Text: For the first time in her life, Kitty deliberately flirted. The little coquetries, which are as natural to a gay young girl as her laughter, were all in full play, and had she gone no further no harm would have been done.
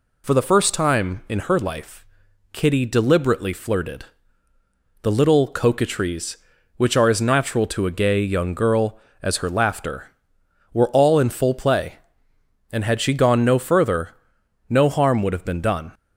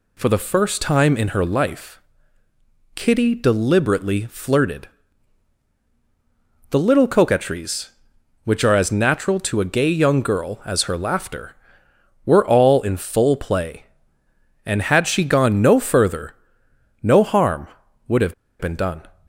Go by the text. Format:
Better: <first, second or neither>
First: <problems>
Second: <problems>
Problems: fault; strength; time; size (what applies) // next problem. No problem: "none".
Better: first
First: pauses between "further" and "no"; noticeable; at 14.1 s; 0.56 s long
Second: pauses between "further" and "no"; noticeable; at 16.3 s; 0.66 s long // pauses between "have" and "been"; slight; at 18.3 s; 0.25 s long